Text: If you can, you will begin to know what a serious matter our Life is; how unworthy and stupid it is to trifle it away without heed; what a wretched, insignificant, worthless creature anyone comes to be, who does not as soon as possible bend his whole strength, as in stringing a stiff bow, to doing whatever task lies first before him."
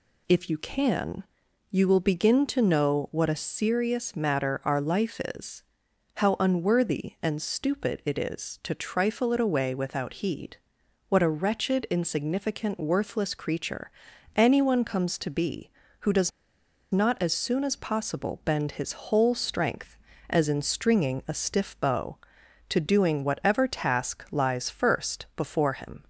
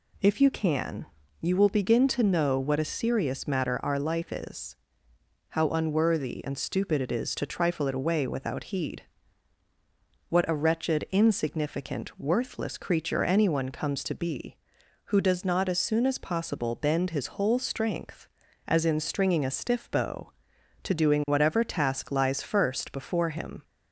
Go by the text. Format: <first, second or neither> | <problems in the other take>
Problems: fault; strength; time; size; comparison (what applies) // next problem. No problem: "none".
second | pauses between "creature" and "anyone"; at 13.9 s; 0.44 s long // pauses between "does" and "not"; noticeable; at 16.3 s; 0.61 s long